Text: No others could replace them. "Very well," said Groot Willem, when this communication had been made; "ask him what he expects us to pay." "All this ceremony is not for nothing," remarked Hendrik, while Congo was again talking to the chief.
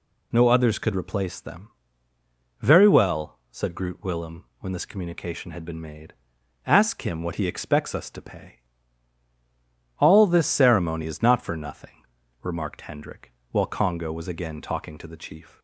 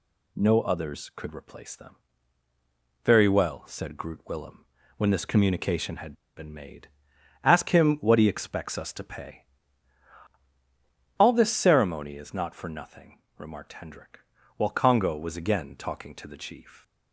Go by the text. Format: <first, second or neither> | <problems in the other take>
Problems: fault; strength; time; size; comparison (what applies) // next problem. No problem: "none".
first | pauses between "had" and "been"; slight; at 6.1 s; 0.22 s long